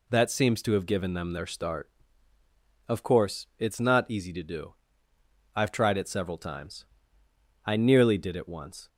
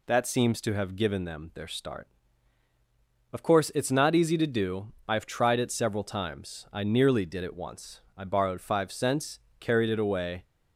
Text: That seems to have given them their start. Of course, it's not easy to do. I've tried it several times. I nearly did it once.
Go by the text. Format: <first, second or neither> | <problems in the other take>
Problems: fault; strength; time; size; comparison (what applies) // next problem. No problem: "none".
first | goes on to say "I borrowed five cents carried it away"; strong; from 8.1 s on; 2.2 s long